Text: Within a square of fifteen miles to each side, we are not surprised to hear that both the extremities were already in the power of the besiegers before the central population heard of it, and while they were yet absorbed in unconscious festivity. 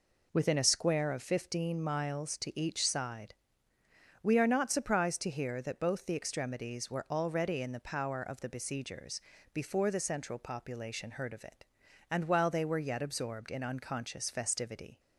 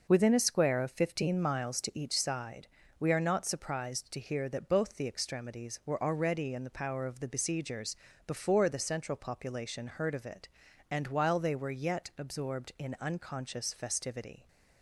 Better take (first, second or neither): neither